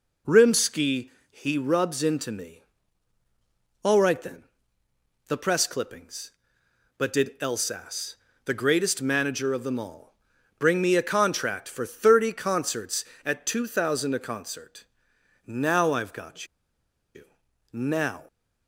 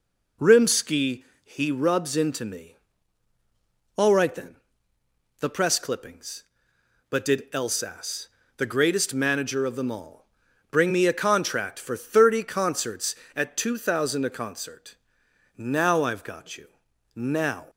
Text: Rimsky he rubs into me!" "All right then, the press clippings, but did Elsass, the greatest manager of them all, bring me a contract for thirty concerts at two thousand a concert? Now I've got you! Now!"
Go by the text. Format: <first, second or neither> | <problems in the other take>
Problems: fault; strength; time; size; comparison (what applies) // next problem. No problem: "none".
second | pauses between "Rimsky" and "he"; slight; at 1.1 s; 0.18 s long; slight in the second // pauses between "got" and "you"; noticeable; at 16.4 s; 0.68 s long